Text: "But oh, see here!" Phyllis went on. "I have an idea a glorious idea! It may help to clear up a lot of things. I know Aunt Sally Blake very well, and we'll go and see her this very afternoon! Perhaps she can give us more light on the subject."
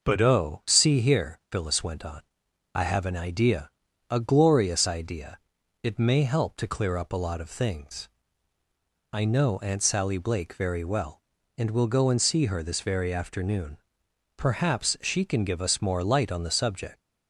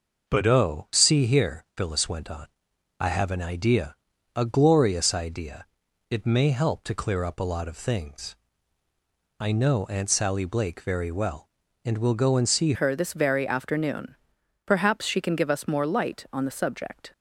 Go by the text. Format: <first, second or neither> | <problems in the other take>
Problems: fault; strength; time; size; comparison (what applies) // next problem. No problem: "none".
first | pauses between "idea" and "a"; at 3.9 s; 0.40 s long; also in the first // changes voice at "her"; from 12.7 s on; 4.4 s long